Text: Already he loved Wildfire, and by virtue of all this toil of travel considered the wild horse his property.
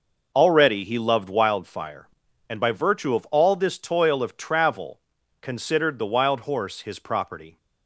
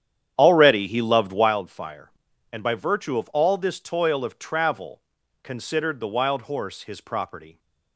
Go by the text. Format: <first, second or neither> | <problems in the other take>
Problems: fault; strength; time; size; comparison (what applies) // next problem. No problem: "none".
first | starts louder than the rest; strong; until 1.5 s; 9.5 dB // pauses between "travel" and "considered"; at 4.9 s; 0.44 s long; also in the first